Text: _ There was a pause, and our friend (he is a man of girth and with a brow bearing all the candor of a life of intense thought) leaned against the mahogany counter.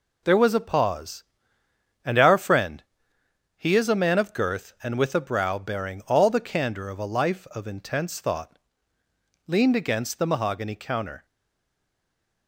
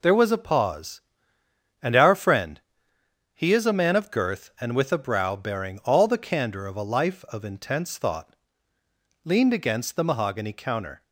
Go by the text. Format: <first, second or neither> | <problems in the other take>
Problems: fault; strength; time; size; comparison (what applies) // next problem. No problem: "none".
second | stays silent after the last word; noticeable; from 11.2 s on; 1.2 s long